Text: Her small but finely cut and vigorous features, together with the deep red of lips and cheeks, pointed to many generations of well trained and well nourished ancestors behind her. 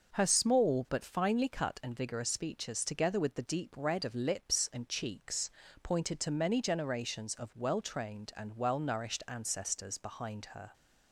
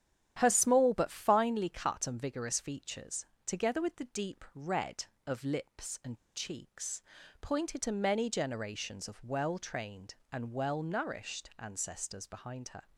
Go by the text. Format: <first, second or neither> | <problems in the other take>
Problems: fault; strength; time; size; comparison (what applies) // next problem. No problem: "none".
first | starts louder than the rest; strong; until 1.3 s; 10 dB // pauses between "and" and "cheeks"; slight; at 6.1 s; 0.20 s long